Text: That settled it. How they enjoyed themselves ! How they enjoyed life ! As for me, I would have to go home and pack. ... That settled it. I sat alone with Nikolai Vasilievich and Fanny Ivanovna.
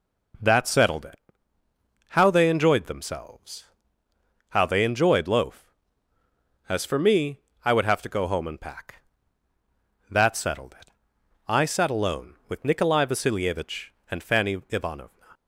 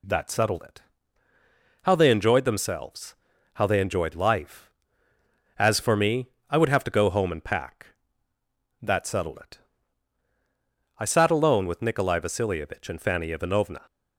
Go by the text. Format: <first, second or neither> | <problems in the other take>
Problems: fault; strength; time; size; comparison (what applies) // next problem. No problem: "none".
second | says "loaf" for "life"; at 5.2 s